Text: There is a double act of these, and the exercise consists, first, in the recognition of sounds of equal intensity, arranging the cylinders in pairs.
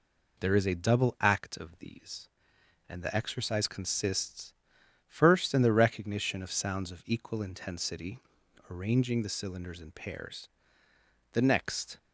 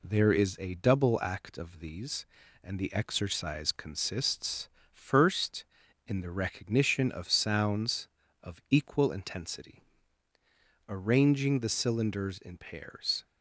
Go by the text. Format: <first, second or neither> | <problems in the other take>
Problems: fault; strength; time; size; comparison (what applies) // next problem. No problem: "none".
second | goes on to say "The next"; noticeable; from 11.3 s on; 0.64 s long